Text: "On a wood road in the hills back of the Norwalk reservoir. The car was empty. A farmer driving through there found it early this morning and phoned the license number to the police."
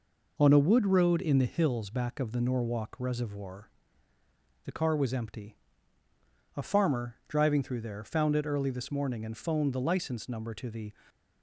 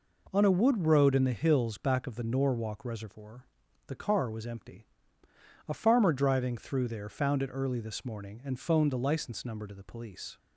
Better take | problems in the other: second | stops before "police"; at 11.0 s

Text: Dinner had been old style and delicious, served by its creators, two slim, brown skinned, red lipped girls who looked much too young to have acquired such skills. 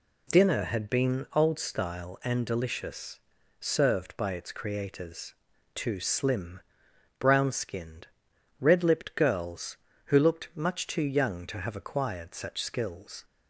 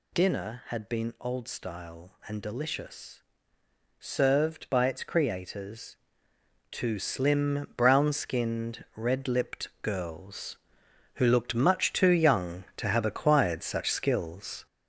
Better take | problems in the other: first | gets louder; noticeable; throughout; 6 dB

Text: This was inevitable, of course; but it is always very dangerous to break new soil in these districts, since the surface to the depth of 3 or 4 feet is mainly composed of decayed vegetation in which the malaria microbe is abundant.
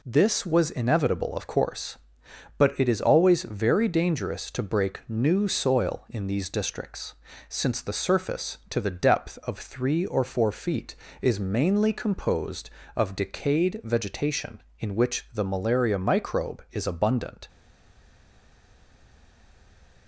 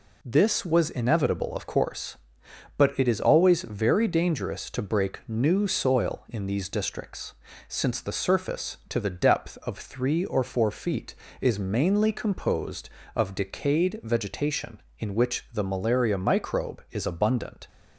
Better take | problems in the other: second | stays silent after the last word; strong; from 17.4 s on; 2.6 s long

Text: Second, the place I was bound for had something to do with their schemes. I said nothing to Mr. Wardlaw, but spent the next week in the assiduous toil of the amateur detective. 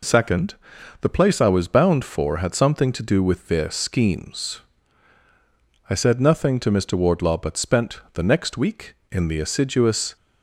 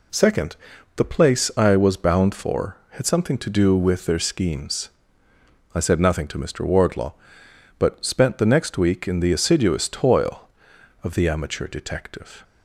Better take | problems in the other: second | stops before "toil of the amateur detective"; at 10.1 s

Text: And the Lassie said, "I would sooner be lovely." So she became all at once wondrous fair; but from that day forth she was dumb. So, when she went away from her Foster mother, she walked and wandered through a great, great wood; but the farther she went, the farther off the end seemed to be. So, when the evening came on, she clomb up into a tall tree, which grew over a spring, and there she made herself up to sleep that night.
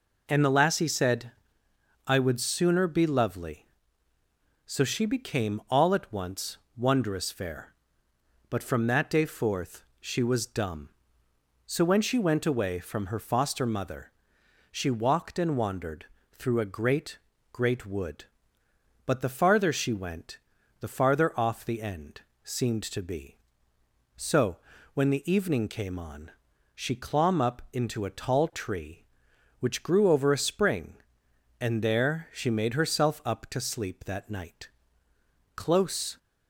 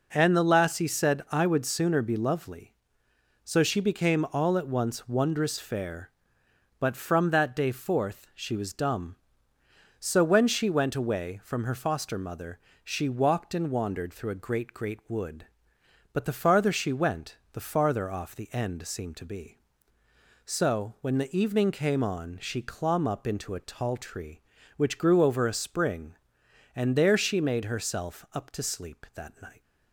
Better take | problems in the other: second | pauses between "once" and "wondrous"; slight; at 6.5 s; 0.18 s long // pauses between "forth" and "she"; slight; at 9.8 s; 0.16 s long // pauses between "wandered" and "through"; slight; at 16.0 s; 0.28 s long // pauses between "end" and "seemed"; slight; at 22.2 s; 0.22 s long // goes on to say "Close"; noticeable; from 35.5 s on; 0.62 s long

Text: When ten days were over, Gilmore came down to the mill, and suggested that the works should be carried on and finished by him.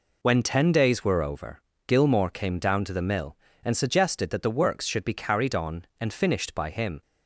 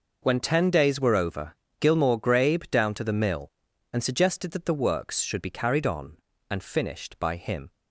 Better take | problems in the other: first | says "grabe" for "came"; at 2.1 s

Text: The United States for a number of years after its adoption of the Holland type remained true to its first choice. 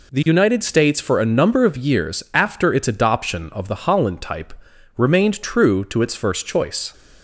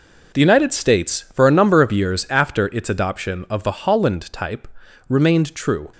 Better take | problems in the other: first | pauses between "type" and "remained"; at 4.6 s; 0.42 s long; noticeable in the first // stops before "to its first choice"; at 5.9 s

